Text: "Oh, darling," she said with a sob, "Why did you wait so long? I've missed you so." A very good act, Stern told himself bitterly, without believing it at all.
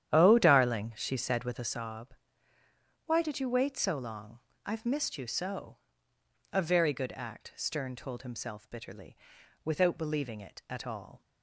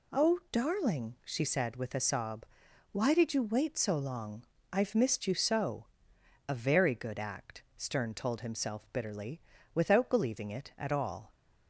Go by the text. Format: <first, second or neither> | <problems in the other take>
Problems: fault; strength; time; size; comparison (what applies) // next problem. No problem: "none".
second | starts louder than the rest; strong; until 1.9 s; 10.5 dB